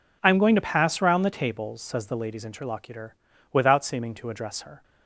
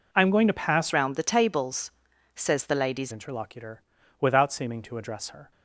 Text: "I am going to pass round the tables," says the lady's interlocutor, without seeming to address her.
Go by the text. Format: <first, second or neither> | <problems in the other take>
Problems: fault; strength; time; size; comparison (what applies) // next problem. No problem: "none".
first | changes voice from "round" to "lady's"; from 0.9 to 3.1 s; 2.2 s long